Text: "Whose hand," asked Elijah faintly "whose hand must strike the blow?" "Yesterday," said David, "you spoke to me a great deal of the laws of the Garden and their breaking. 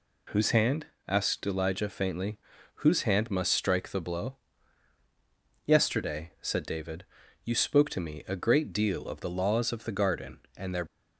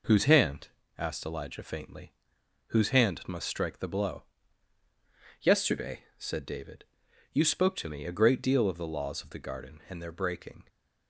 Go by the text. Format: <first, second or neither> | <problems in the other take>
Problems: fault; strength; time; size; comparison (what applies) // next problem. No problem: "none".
second | pauses between "faintly" and "whose"; at 2.3 s; 0.44 s long; noticeable in the second // stops before "breaking"; at 10.8 s